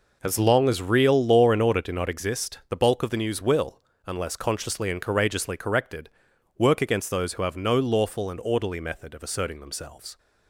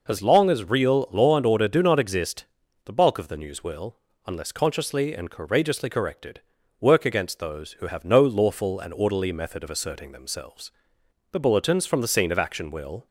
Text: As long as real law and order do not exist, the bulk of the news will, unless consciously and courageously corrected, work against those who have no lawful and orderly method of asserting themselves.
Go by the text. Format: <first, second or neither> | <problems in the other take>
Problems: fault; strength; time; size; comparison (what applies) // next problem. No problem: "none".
first | goes on to say "The bulletins from the scene of action will"; strong; from 11.3 s on; 1.7 s long